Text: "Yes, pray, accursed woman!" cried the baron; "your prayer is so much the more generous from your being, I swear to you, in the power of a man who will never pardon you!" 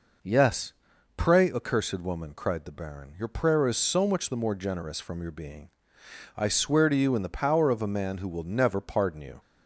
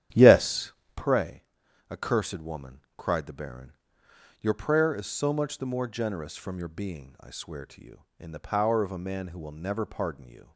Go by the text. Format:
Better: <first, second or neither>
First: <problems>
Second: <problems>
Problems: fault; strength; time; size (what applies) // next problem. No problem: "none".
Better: first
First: none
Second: starts louder than the rest; strong; until 1.1 s; 10.5 dB